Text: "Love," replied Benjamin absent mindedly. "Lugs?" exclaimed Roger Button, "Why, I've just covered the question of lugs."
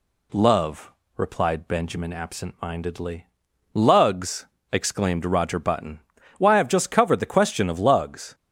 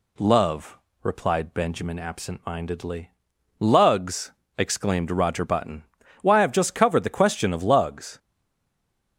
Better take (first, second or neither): first